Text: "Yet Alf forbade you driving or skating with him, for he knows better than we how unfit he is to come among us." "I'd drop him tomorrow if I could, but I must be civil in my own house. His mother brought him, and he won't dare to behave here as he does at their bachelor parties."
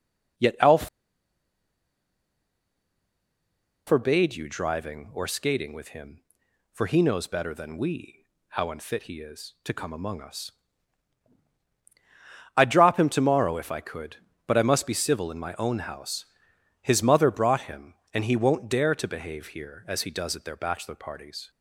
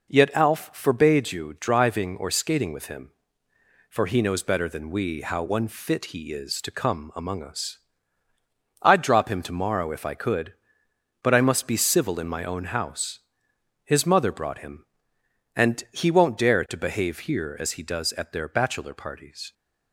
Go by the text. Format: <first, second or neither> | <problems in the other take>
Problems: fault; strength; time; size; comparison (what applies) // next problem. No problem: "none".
second | pauses between "Alf" and "forbade"; strong; at 0.8 s; 3.0 s long // pauses between "we" and "how"; slight; at 8.2 s; 0.24 s long